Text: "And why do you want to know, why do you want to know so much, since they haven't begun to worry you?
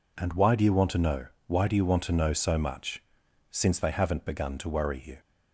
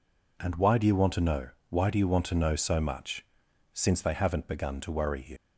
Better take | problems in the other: first | leaves "you" unfinished; at 5.3 s; 60 ms

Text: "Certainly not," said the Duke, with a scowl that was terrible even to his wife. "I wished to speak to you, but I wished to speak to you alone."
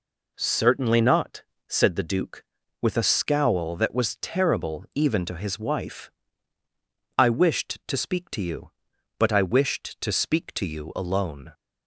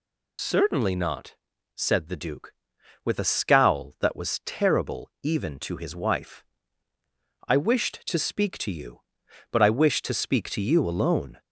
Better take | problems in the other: first | loses the start of "Certainly"; at 0.3 s; 75 ms

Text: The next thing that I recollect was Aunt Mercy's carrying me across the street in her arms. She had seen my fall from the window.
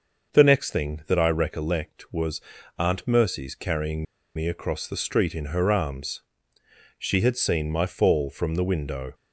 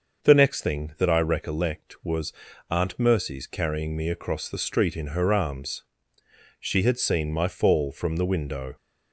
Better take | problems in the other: second | starts louder than the rest; until 1.3 s; 6 dB; also in the second // pauses between "was" and "Aunt"; at 2.3 s; 0.38 s long; also in the second // pauses between "carrying" and "me"; slight; at 4.0 s; 0.31 s long

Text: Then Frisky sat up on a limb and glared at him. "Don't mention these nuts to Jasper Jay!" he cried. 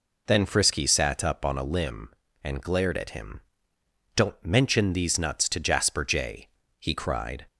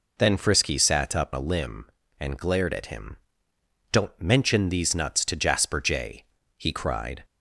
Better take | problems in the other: first | skips "on"; at 1.3 s

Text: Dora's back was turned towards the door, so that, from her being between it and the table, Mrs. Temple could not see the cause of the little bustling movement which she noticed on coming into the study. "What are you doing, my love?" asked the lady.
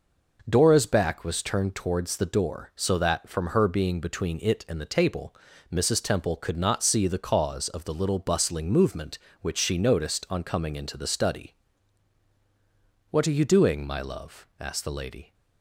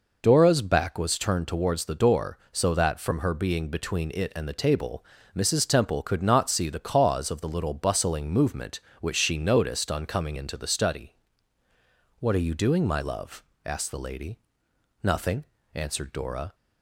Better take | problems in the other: first | goes on to say "Nothing answered Dora"; from 15.0 s on; 1.5 s long

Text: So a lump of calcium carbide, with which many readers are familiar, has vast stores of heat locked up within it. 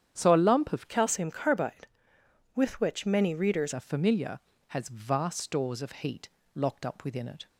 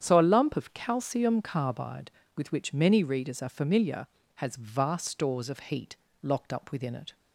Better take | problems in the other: second | starts louder than the rest; strong; until 1.1 s; 9 dB; strong in the second // changes voice from "calcium" to "readers"; from 0.8 to 3.7 s; 2.9 s long // pauses between "heat" and "locked"; slight; at 6.2 s; 0.26 s long; slight in the second

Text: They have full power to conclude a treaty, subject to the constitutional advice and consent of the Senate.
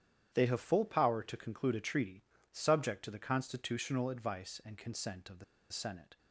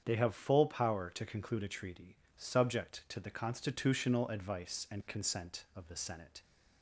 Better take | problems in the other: second | starts louder than the rest; strong; until 1.3 s; 9.5 dB; strong in the second // pauses between "the" and "Senate"; slight; at 5.4 s; 0.27 s long

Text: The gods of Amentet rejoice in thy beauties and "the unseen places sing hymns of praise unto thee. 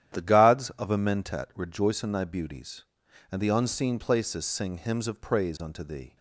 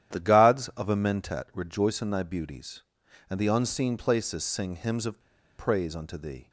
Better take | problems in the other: first | starts louder than the rest; strong; until 1.2 s; 11 dB; strong in the first // pauses between "of" and "praise"; at 5.1 s; 0.39 s long

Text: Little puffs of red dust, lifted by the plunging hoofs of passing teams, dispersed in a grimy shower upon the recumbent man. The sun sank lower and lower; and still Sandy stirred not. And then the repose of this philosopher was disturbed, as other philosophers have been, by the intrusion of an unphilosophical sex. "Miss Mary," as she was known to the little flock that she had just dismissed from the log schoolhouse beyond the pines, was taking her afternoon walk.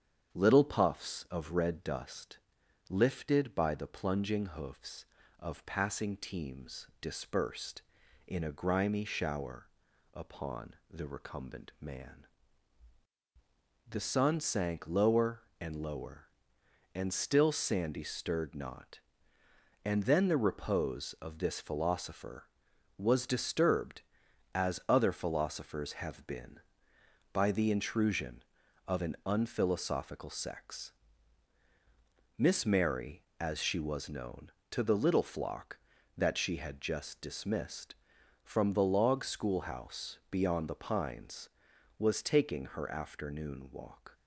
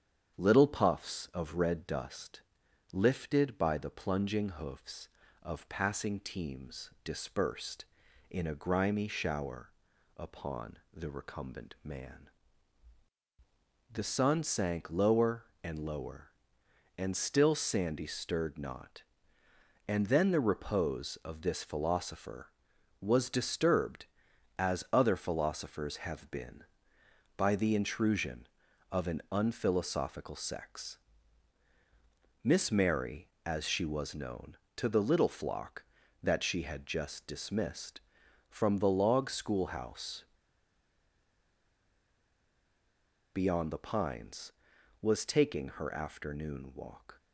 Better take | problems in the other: first | starts louder than the rest; strong; until 1.4 s; 8.5 dB; strong in the first // pauses between "shower" and "upon"; noticeable; at 9.6 s; 0.46 s long; noticeable in the first // pauses between "schoolhouse" and "beyond"; strong; at 40.2 s; 3.0 s long

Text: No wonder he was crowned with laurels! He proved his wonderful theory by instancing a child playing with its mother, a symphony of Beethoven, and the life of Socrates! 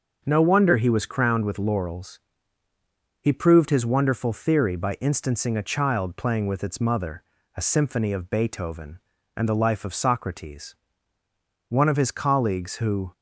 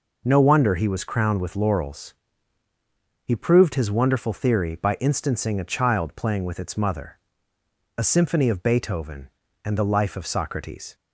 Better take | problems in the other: second | starts louder than the rest; until 1.2 s; 6.5 dB // goes on to say "One of his colleagues who"; from 11.6 s on; 1.4 s long

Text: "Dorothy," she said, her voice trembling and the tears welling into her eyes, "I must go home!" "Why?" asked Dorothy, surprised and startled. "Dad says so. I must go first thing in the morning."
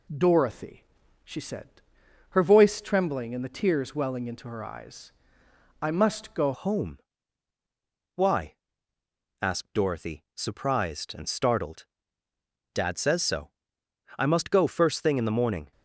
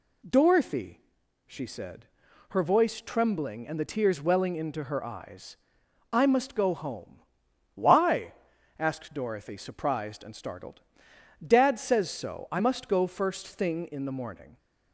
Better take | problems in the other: second | changes voice at "home"; from 6.5 s on; 9.2 s long

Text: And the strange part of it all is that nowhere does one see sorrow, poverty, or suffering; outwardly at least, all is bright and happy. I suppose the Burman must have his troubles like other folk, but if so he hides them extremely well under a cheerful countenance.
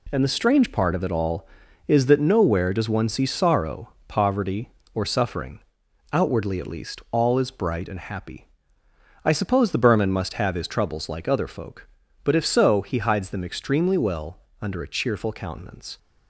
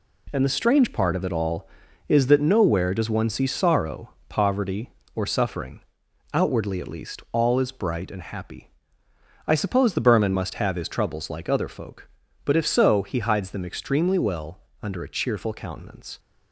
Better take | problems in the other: neither | pauses between "well" and "under"; slight; the same in both

